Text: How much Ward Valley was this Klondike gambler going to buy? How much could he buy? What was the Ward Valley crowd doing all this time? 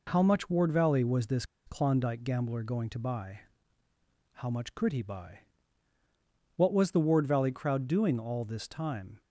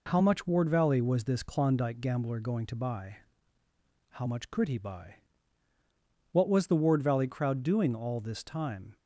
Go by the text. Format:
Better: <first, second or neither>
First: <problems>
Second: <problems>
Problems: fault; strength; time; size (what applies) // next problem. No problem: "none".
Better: second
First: pauses between "this" and "Klondike"; slight; at 1.4 s; 0.22 s long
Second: none